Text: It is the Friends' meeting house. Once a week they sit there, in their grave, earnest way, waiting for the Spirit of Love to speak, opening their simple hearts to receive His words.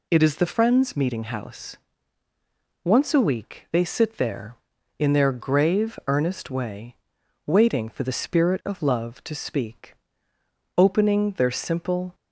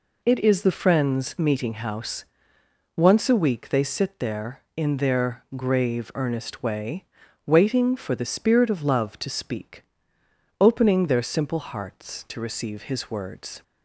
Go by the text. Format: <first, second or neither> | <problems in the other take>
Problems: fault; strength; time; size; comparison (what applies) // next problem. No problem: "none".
second | stops before "hearts to receive His words"; at 12.1 s